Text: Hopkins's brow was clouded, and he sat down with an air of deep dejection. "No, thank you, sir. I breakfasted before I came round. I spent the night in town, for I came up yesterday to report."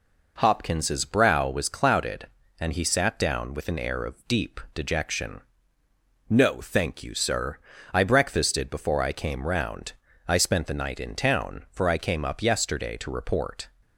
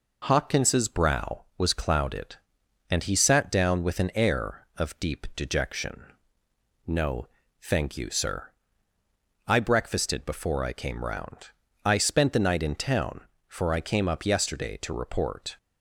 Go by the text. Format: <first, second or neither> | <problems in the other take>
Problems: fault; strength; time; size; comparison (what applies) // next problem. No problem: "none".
neither | none